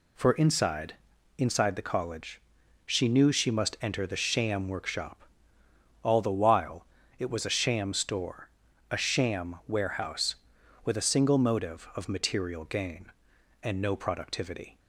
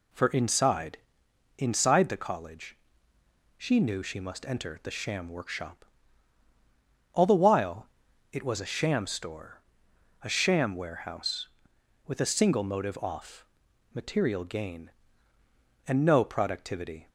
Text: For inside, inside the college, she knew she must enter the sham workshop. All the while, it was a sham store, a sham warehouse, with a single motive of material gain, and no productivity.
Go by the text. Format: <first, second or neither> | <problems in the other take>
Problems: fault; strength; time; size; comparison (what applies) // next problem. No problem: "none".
first | says "off" for "of"; at 12.9 s